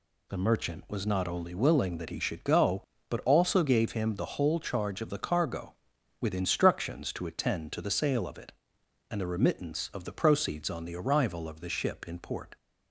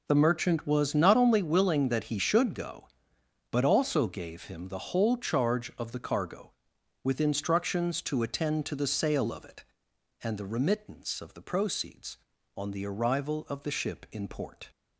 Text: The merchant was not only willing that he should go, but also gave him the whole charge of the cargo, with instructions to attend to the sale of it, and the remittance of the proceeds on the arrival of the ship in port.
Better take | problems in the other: neither | none

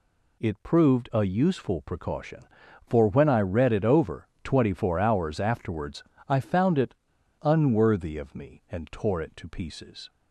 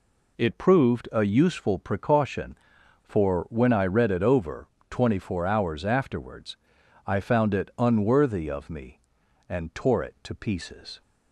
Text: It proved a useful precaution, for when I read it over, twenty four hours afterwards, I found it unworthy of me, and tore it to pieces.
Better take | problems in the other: second | pauses between "it" and "unworthy"; noticeable; at 6.9 s; 0.48 s long

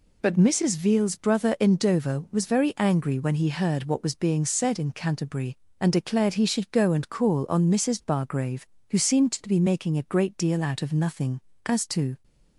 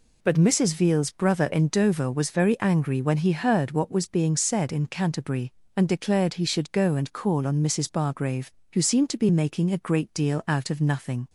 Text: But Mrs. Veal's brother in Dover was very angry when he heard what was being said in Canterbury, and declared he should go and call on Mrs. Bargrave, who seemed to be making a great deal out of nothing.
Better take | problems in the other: second | goes on to say "As to"; from 11.6 s on; 0.58 s long

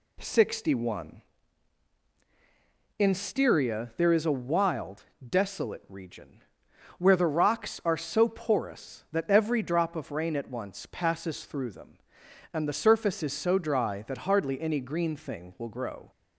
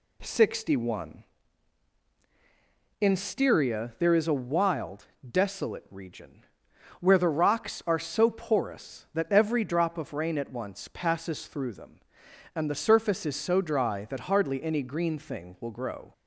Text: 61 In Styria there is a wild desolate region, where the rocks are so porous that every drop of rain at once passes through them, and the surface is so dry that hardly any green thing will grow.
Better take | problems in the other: neither | pauses between "wild" and "desolate"; slight; the same in both

